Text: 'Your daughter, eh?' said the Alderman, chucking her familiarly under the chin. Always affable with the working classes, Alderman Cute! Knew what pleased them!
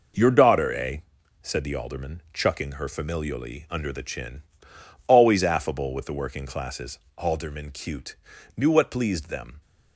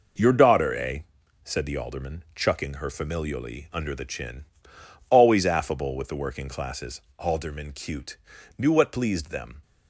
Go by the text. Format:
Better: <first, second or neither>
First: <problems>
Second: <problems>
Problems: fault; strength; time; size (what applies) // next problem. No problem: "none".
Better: neither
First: none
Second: none